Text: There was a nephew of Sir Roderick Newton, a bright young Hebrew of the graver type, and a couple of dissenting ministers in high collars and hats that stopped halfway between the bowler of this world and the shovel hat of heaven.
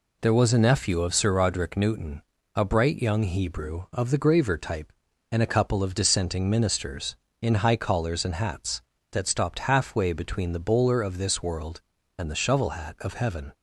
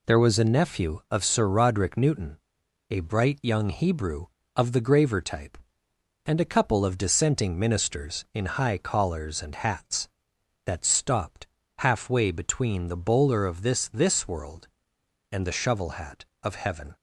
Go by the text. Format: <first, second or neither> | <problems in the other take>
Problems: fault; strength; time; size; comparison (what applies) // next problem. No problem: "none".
first | pauses between "stopped" and "halfway"; slight; at 11.4 s; 0.32 s long // says "this" twice; at 13.8 s